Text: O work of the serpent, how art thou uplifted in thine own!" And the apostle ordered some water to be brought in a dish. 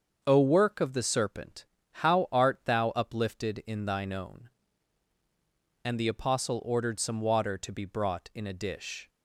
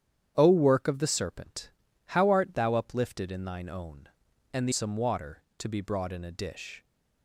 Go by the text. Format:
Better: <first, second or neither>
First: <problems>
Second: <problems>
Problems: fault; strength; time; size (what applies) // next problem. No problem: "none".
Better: first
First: starts louder than the rest; until 1.2 s; 6.5 dB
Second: starts louder than the rest; strong; until 1.3 s; 9.5 dB // skips "apostle ordered"; at 4.7 s